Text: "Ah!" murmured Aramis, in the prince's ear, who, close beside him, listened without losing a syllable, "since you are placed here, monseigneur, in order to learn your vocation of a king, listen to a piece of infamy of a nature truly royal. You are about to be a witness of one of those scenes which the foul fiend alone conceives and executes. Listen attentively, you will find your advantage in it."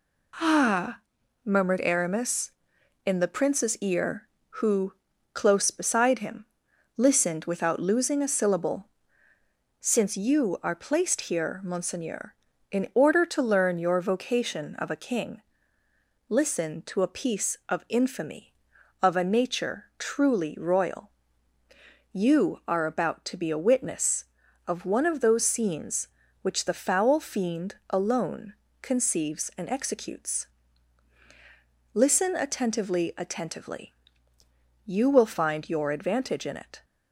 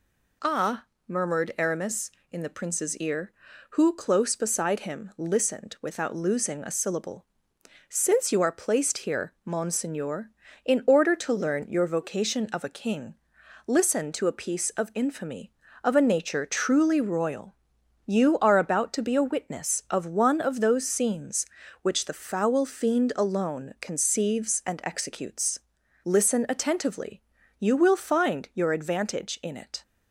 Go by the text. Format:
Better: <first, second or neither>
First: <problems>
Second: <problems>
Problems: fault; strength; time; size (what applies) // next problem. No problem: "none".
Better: second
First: pauses between "fiend" and "alone"; slight; at 27.7 s; 0.16 s long // pauses between "alone" and "conceives"; slight; at 28.5 s; 0.26 s long // says "attentively" twice; at 33.1 s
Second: none